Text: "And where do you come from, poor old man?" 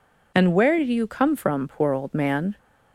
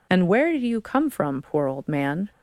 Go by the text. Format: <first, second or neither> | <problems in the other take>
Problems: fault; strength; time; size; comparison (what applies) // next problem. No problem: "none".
neither | none